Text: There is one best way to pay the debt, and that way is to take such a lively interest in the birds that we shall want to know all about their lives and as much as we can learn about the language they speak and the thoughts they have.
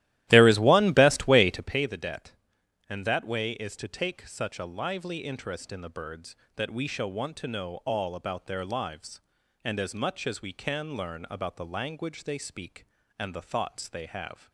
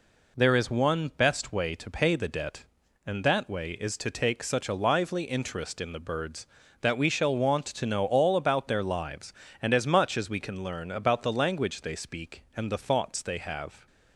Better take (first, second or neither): second